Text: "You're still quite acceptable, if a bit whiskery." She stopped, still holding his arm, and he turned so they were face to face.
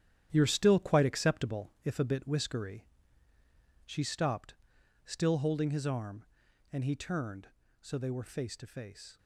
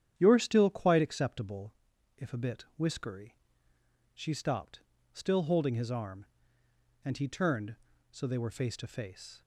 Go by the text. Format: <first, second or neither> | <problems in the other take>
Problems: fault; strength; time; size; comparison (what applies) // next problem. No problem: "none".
second | gets quieter; strong; throughout; 8.5 dB // starts louder than the rest; strong; until 1.3 s; 10.5 dB; strong in the second